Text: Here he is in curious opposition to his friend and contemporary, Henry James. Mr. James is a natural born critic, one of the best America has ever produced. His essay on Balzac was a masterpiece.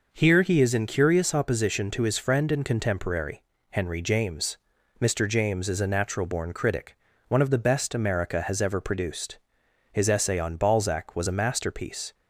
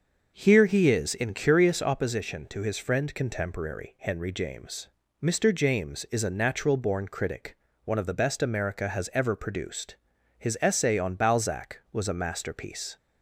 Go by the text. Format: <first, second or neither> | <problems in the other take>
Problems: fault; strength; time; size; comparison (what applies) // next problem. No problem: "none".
first | starts louder than the rest; until 1.3 s; 6 dB // skips "and"; at 3.1 s